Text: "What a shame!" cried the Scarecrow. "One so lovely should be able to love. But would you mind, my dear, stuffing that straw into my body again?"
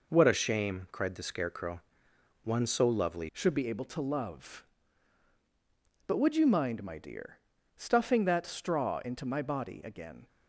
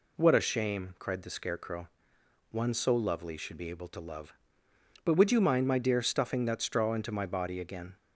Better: second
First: changes voice at "should"; from 3.3 s on; 6.9 s long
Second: none

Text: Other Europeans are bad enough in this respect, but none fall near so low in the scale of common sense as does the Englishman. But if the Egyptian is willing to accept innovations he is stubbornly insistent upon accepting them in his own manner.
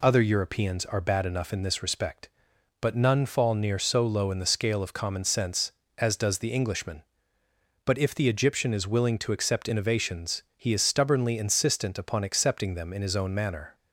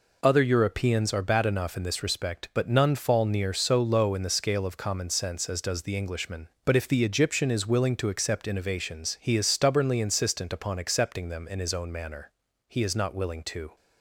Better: first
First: none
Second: goes on to say "He is not willing to"; noticeable; from 12.6 s on; 1.0 s long

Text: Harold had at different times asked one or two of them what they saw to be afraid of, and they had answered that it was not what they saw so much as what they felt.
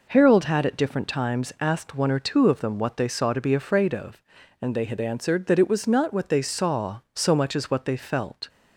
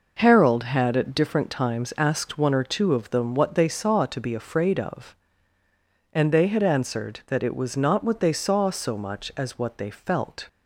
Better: neither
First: none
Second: none

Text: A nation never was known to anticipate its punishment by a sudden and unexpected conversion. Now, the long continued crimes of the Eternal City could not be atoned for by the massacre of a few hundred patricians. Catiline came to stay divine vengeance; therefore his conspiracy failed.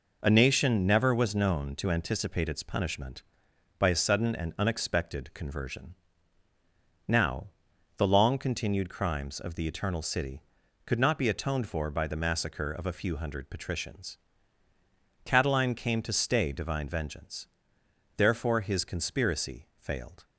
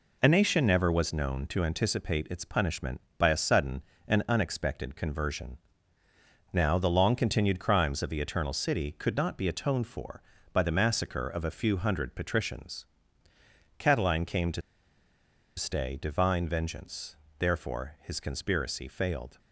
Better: first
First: none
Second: pauses between "to" and "stay"; noticeable; at 14.6 s; 0.96 s long

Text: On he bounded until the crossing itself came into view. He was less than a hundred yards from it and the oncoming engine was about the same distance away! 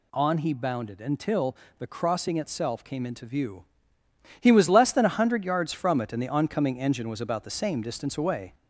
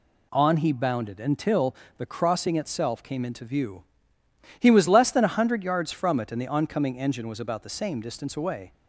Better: second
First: gets louder; slight; throughout; 2 dB // pauses between "until" and "the"; slight; at 1.5 s; 0.22 s long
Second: pauses between "until" and "the"; slight; at 1.7 s; 0.22 s long

